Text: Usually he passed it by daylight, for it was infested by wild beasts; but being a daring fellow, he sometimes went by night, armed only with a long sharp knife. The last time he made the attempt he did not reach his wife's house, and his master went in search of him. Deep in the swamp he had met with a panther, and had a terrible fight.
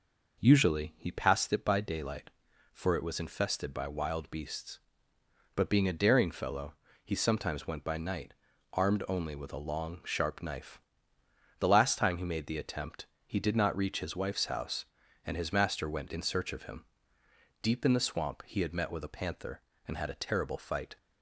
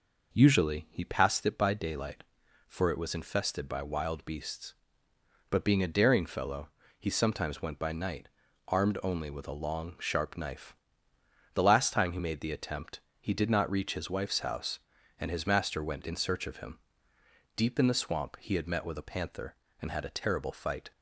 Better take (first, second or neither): neither